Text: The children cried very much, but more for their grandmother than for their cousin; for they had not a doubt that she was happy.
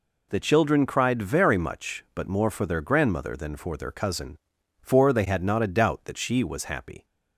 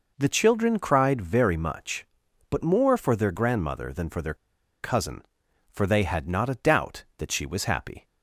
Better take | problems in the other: first | pauses between "their" and "cousin"; noticeable; at 4.3 s; 0.48 s long

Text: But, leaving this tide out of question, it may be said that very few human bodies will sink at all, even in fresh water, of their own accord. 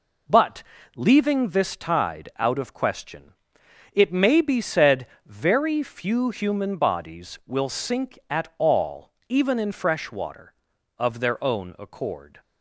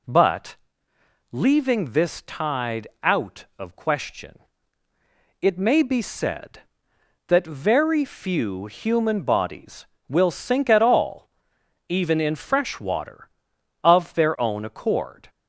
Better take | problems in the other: second | skips "that"; at 5.1 s

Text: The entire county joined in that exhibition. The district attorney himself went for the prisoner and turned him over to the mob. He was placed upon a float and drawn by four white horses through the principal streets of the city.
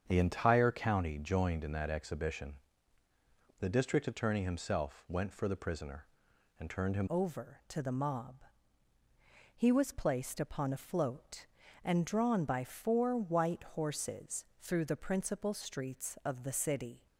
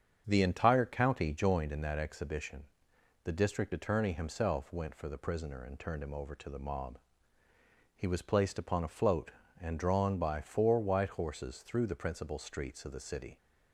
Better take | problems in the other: second | starts louder than the rest; strong; until 1.0 s; 7 dB; strong in the second // changes voice at "over"; from 7.1 s on; 9.9 s long // pauses between "horses" and "through"; slight; at 14.4 s; 0.16 s long

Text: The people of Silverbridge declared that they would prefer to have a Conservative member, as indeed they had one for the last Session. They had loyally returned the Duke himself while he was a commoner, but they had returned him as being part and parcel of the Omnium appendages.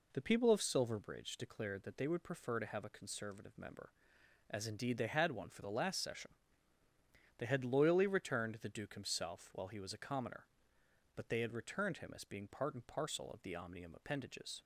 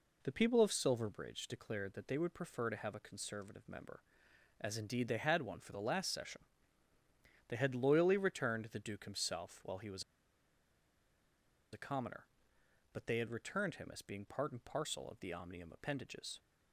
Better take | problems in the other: first | pauses between "was" and "a"; strong; at 10.0 s; 1.7 s long

